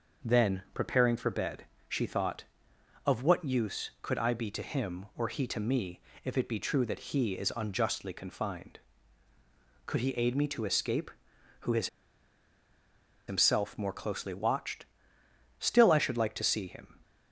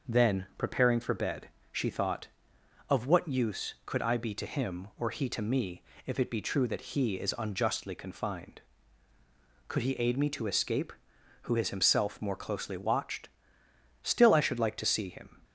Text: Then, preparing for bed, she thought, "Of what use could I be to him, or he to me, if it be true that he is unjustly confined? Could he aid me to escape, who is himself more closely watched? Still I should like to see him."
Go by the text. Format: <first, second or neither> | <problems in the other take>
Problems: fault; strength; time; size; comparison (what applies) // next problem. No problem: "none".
second | pauses between "is" and "himself"; strong; at 11.8 s; 1.3 s long